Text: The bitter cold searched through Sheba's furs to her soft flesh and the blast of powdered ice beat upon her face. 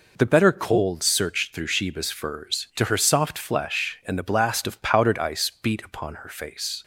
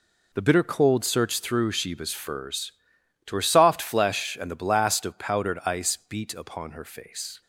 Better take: second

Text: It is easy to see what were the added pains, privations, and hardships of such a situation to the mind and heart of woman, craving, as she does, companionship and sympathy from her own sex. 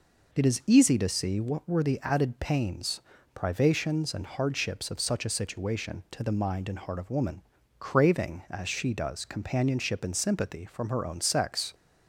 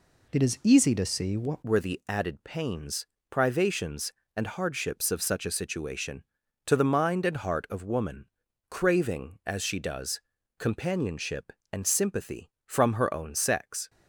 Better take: first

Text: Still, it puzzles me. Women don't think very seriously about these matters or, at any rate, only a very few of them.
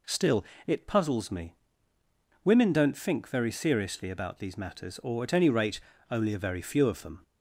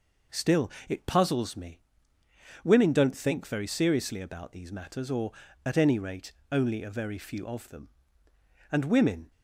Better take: first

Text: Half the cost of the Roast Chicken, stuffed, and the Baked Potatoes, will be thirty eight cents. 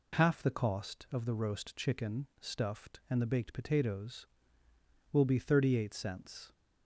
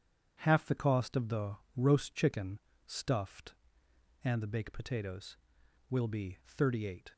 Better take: first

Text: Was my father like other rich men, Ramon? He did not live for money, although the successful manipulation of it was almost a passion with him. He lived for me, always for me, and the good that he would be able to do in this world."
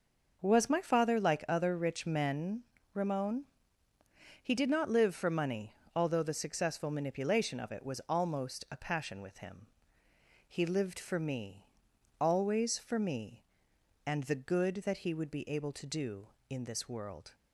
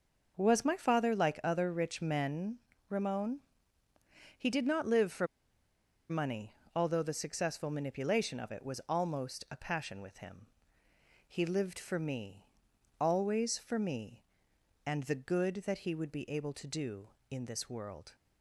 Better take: first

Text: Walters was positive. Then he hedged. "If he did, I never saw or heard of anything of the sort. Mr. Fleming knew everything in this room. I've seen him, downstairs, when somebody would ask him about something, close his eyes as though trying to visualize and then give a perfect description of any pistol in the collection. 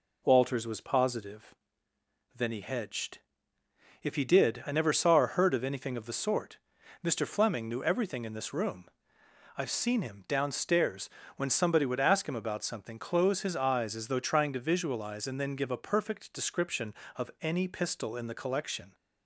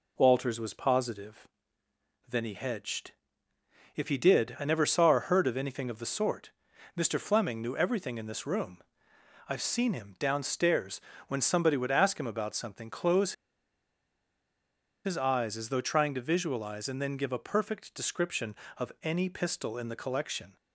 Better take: first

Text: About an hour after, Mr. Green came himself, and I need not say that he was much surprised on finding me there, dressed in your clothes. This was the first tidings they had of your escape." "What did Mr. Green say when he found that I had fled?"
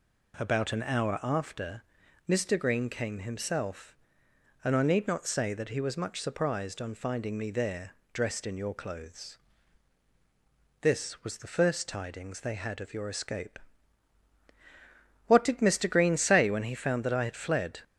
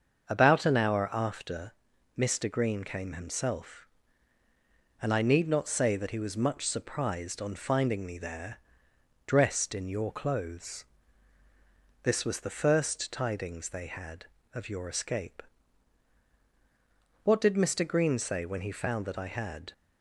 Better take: first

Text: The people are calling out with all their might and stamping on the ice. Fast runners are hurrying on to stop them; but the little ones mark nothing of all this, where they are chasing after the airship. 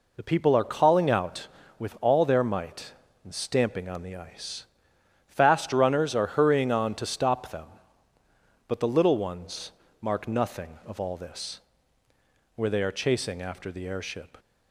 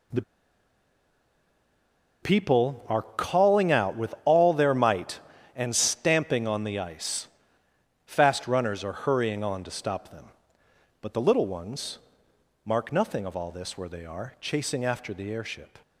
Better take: first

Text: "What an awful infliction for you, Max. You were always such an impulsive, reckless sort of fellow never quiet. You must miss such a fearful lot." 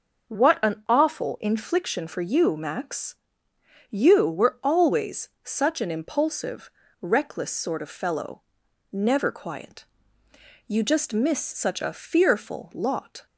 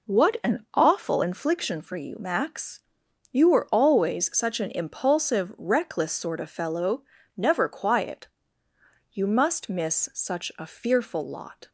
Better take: second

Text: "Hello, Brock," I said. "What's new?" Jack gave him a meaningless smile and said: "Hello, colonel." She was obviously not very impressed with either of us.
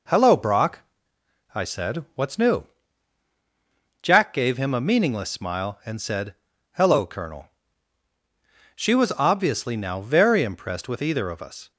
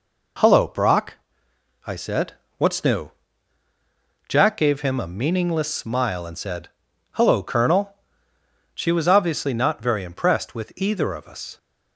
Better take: second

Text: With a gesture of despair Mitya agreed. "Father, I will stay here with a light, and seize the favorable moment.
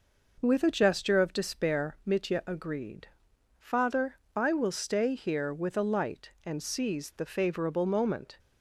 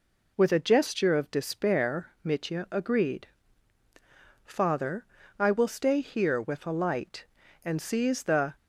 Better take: first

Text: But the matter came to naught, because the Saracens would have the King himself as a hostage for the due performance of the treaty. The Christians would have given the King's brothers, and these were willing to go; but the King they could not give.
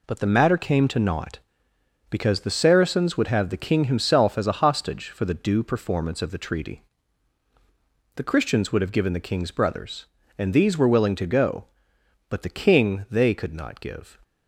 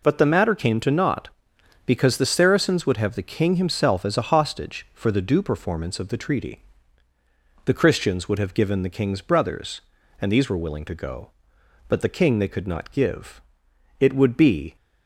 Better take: first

